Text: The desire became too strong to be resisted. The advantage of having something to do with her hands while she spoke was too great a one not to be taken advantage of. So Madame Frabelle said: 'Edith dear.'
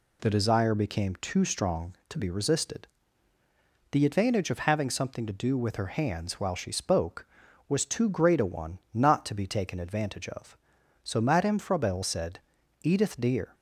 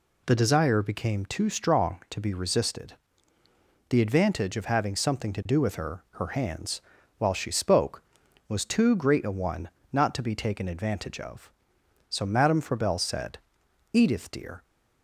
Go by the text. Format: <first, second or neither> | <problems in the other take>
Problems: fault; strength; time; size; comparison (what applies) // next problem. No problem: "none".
first | says "her" twice; at 6.1 s // pauses between "hands" and "while"; at 6.8 s; 0.38 s long // pauses between "one" and "not"; slight; at 9.6 s; 0.24 s long; slight in the first